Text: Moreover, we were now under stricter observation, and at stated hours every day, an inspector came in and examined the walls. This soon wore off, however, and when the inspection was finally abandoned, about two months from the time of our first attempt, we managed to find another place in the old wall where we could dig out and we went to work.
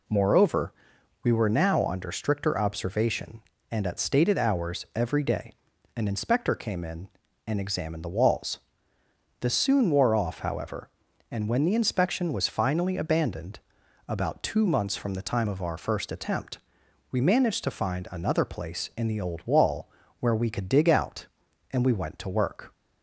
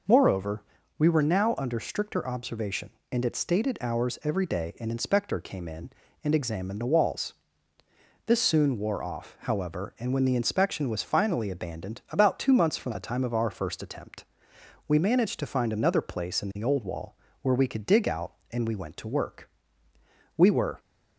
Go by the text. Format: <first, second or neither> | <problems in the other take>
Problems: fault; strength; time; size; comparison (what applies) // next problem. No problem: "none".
first | pauses between "wall" and "where"; slight; at 17.1 s; 0.28 s long; slight in the first // goes on to say "We were"; slight; from 20.3 s on; 0.42 s long